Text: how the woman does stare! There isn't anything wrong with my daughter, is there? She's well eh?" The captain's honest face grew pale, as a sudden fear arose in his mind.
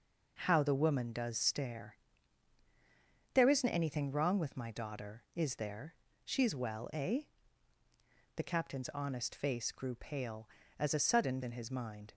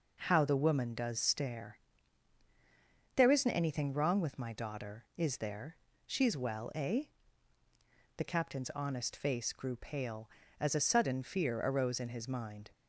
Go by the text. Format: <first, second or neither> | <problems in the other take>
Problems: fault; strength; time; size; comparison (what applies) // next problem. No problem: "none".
second | skips "fear arose"; at 11.4 s